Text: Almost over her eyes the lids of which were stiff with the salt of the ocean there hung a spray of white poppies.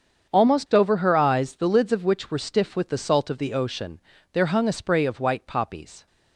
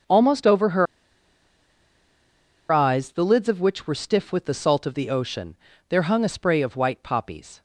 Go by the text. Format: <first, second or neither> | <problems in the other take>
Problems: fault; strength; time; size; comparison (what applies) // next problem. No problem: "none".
first | starts louder than the rest; strong; until 2.9 s; 7 dB; strong in the first // pauses between "her" and "eyes"; strong; at 0.8 s; 1.8 s long // pauses between "ocean" and "there"; slight; at 5.5 s; 0.32 s long; slight in the first